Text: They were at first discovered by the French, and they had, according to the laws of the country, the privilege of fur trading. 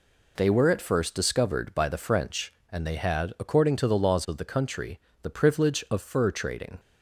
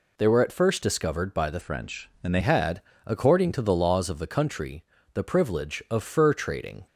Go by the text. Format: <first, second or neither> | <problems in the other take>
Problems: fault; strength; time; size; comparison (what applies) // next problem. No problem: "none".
first | changes voice from "French" to "they"; from 1.6 to 2.3 s; 0.7 s long